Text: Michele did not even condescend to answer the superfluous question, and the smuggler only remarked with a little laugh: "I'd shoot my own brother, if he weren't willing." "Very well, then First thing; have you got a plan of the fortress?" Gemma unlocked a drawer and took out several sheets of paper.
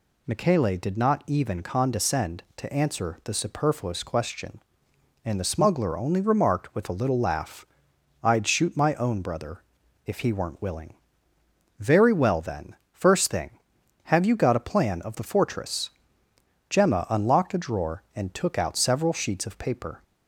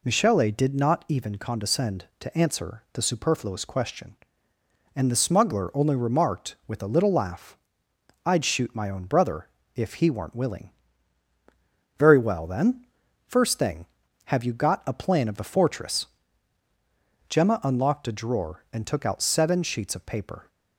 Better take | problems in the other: first | pauses between "then" and "First"; at 12.8 s; 0.42 s long; slight in the first // says "seven" for "several"; at 19.2 s

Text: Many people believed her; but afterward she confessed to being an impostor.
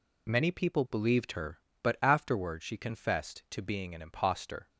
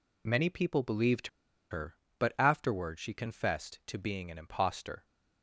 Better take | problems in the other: first | pauses between "believed" and "her"; at 1.2 s; 0.42 s long

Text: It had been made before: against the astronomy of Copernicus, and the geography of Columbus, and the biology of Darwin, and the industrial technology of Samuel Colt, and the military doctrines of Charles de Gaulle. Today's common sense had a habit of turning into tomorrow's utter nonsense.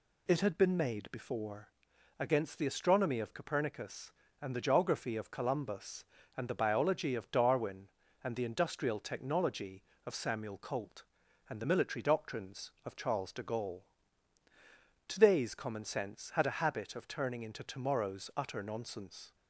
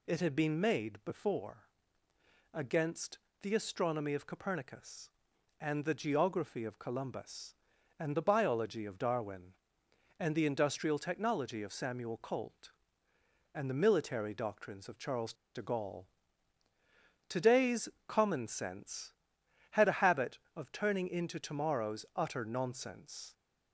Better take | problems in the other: first | pauses between "against" and "the"; slight; at 3.1 s; 0.24 s long // pauses between "Charles" and "de"; slight; at 15.3 s; 0.21 s long // pauses between "Today's" and "common"; slight; at 17.8 s; 0.18 s long

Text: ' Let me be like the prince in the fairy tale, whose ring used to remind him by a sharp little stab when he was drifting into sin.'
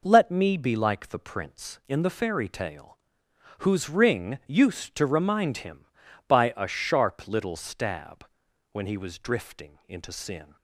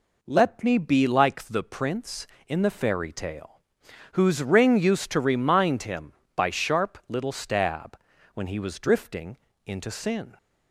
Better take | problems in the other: first | skips "a"; at 6.5 s // pauses between "stab" and "when"; slight; at 7.9 s; 0.36 s long; noticeable in the first // pauses between "drifting" and "into"; slight; at 9.3 s; 0.26 s long

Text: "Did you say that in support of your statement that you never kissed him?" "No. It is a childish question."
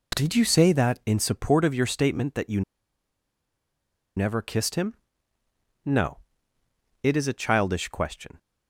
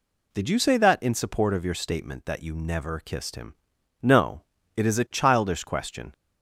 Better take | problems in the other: second | pauses between "you" and "never"; strong; at 2.6 s; 1.5 s long

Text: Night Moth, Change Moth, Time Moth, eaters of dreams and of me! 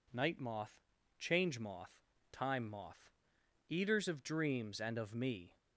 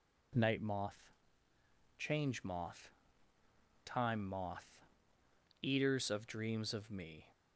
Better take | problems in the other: first | skips "and"; at 6.7 s

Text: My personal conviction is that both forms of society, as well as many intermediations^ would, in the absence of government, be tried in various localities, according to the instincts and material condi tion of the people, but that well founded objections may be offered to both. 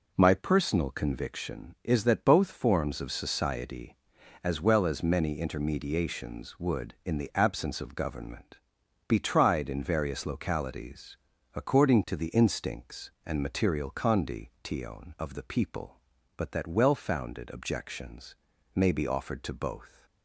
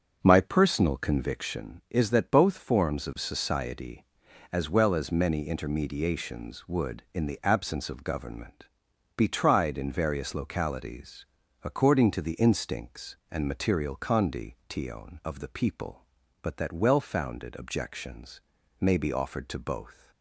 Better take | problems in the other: first | starts louder than the rest; until 1.7 s; 6.5 dB // pauses between "condi" and "tion"; slight; at 14.5 s; 0.16 s long; slight in the first // pauses between "objections" and "may"; at 18.3 s; 0.40 s long; also in the first

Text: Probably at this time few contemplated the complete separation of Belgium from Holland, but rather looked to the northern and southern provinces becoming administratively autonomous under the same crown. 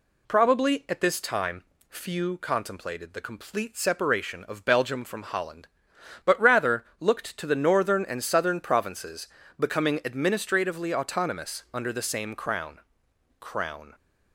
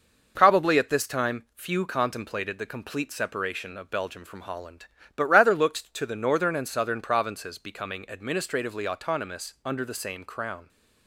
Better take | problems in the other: second | pauses between "time" and "few"; slight; at 1.6 s; 0.26 s long // pauses between "provinces" and "becoming"; slight; at 9.2 s; 0.32 s long // says "crown" twice; at 13.3 s

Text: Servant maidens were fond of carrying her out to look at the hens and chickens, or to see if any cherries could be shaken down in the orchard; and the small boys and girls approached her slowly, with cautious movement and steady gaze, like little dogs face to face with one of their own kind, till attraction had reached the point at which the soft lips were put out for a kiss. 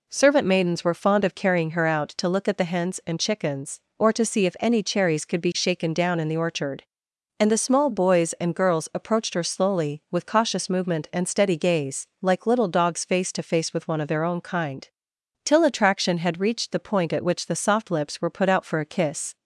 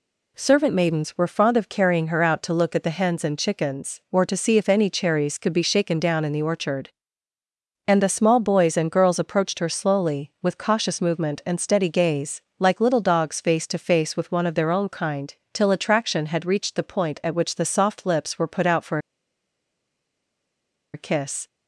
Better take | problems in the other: first | pauses between "for" and "a"; strong; at 18.9 s; 1.9 s long

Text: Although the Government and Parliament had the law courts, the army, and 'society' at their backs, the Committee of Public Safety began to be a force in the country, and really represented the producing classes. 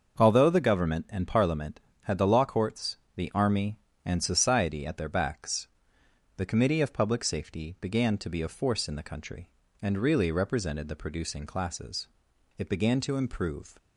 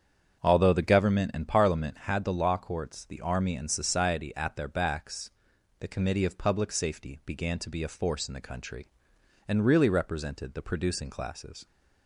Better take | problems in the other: second | starts louder than the rest; until 1.2 s; 6.5 dB; strong in the second // goes on to say "It began to improve"; noticeable; from 12.5 s on; 1.2 s long

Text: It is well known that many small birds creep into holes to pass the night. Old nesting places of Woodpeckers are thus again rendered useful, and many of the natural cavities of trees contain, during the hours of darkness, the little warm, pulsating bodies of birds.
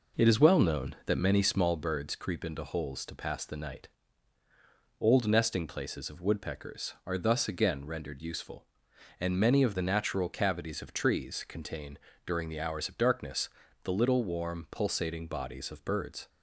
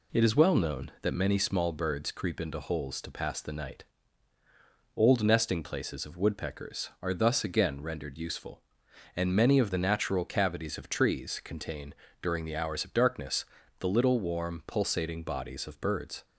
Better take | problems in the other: second | starts louder than the rest; noticeable; until 1.9 s; 4.5 dB

